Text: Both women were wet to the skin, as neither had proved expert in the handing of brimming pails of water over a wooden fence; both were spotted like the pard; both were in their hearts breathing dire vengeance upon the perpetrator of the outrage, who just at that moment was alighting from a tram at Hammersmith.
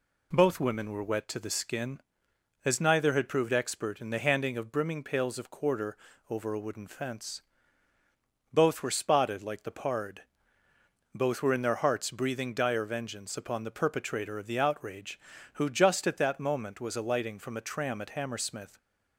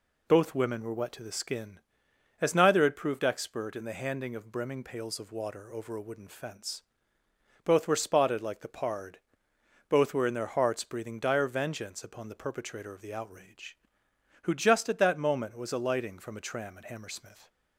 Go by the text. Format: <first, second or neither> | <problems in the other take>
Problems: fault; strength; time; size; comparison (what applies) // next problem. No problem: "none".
second | says "quarter" for "water"; at 5.4 s